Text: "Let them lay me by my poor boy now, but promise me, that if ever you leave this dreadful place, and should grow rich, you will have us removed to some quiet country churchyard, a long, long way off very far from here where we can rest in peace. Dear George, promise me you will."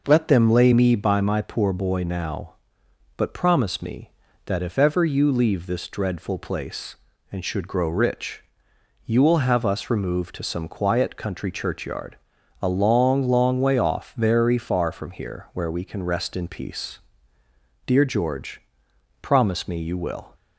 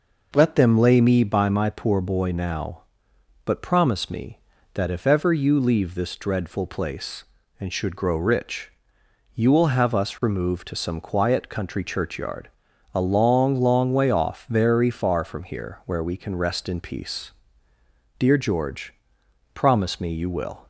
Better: neither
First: none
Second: none

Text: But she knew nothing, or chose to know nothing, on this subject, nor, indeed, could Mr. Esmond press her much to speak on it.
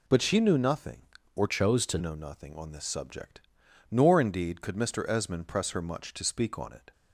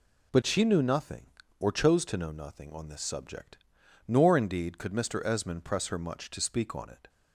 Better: second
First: changes voice from "chose" to "to"; from 1.4 to 1.9 s; 0.5 s long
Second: none

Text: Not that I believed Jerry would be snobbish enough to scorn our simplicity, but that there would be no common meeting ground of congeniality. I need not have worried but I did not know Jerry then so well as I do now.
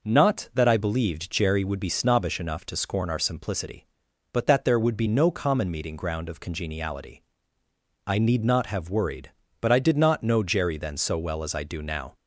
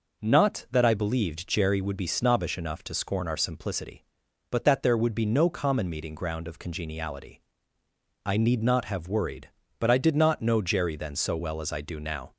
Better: neither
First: none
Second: none

